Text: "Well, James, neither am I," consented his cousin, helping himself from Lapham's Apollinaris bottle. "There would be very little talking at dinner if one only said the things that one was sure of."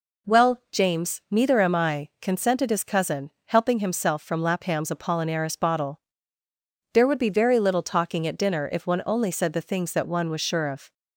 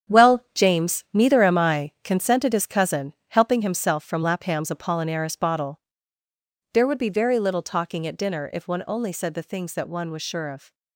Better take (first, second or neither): first